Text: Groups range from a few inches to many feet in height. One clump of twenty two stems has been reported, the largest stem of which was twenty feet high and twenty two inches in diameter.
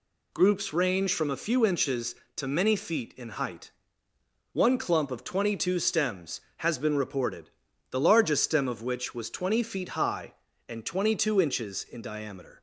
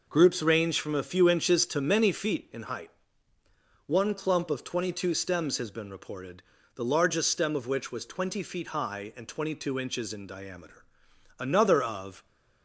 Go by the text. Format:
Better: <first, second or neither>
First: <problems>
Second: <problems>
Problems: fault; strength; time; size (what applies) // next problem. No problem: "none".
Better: first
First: none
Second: goes on to say "Another of"; noticeable; from 11.3 s on; 0.86 s long